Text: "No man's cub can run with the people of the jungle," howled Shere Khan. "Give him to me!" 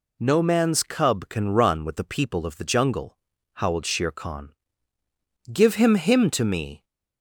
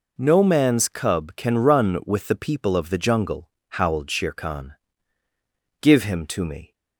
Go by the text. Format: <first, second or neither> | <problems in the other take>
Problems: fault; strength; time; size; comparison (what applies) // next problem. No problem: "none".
second | says "him" twice; at 5.9 s